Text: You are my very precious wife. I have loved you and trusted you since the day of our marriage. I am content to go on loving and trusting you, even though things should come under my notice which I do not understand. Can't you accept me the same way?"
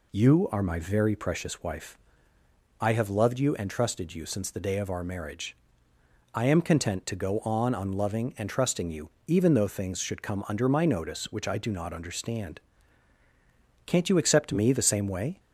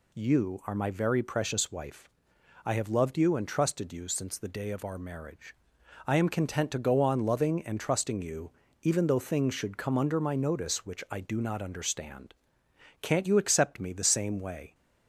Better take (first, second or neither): second